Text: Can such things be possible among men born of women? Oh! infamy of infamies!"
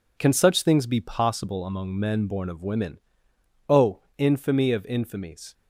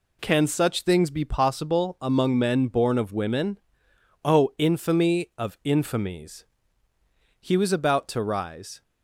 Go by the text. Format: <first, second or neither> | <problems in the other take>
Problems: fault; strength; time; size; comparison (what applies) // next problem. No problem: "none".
first | goes on to say "He was about to rise"; from 7.3 s on; 1.4 s long